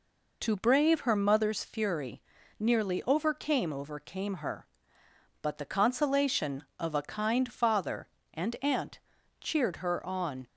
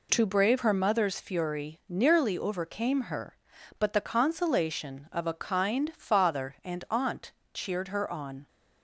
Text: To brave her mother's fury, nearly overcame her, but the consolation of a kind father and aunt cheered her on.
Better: second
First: says "overcame" twice; at 3.7 s // pauses between "aunt" and "cheered"; at 8.9 s; 0.41 s long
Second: pauses between "aunt" and "cheered"; slight; at 7.3 s; 0.20 s long

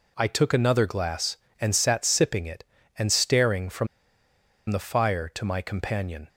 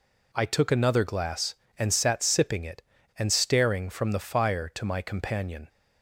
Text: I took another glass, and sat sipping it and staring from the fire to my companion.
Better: second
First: pauses between "from" and "the"; noticeable; at 3.8 s; 0.83 s long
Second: none

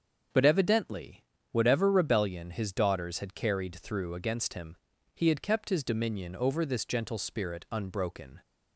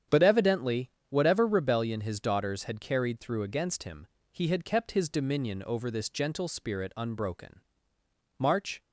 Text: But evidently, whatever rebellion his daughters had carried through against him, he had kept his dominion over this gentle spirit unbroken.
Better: first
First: starts louder than the rest; until 1.6 s; 7 dB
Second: starts louder than the rest; strong; until 1.3 s; 8.5 dB // goes on to say "March"; slight; from 8.3 s on; 0.44 s long

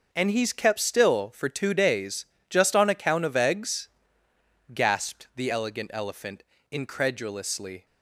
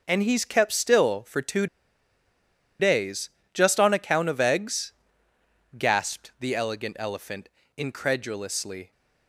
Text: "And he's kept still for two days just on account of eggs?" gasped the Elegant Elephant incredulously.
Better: first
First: pauses between "days" and "just"; slight; at 2.2 s; 0.24 s long // pauses between "Elephant" and "incredulously"; slight; at 6.4 s; 0.28 s long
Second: pauses between "two" and "days"; at 1.6 s; 1.1 s long // pauses between "days" and "just"; slight; at 3.2 s; 0.24 s long // pauses between "Elephant" and "incredulously"; slight; at 7.4 s; 0.28 s long

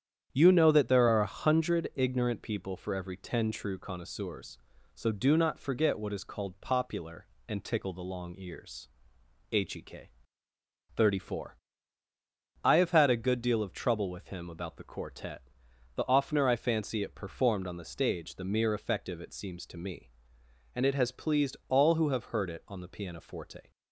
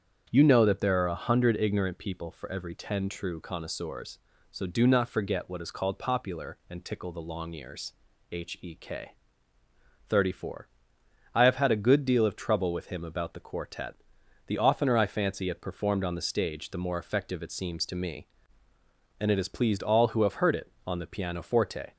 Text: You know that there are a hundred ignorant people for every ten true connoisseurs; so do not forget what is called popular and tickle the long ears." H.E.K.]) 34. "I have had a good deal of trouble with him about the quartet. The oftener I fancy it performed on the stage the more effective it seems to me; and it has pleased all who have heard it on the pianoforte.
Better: second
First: starts louder than the rest; strong; until 1.3 s; 9 dB // says "mere" for "more"; at 18.4 s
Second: starts louder than the rest; strong; until 1.3 s; 7.5 dB

